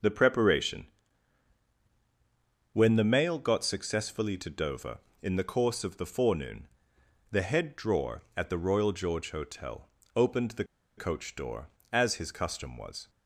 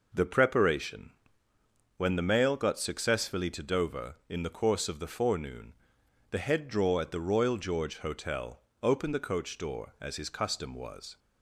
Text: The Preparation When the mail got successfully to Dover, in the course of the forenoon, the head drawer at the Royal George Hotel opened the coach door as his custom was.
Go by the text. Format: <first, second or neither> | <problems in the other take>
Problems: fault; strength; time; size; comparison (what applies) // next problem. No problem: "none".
second | starts louder than the rest; until 2.8 s; 6.5 dB // pauses between "Preparation" and "When"; strong; at 0.8 s; 1.8 s long; noticeable in the second // pauses between "Hotel" and "opened"; slight; at 9.8 s; 0.30 s long; slight in the second // pauses between "the" and "coach"; slight; at 10.6 s; 0.32 s long